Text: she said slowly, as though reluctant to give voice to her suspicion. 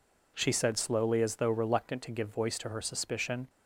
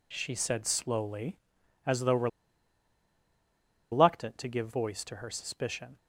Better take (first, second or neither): first